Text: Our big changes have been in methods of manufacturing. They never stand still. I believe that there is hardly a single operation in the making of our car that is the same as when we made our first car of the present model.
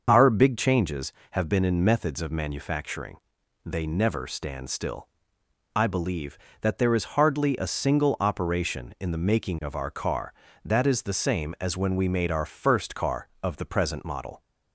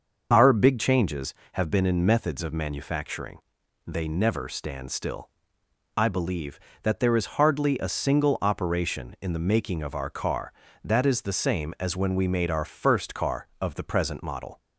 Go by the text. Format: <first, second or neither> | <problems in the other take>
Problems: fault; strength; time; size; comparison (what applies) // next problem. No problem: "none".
neither | starts louder than the rest; the same in both